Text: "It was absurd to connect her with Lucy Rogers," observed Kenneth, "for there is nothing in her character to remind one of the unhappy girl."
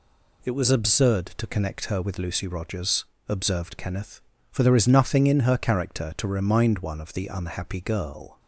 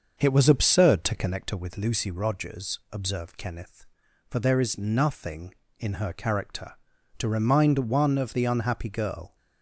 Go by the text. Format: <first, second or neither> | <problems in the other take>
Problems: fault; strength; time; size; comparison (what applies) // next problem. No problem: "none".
first | starts louder than the rest; until 1.4 s; 6.5 dB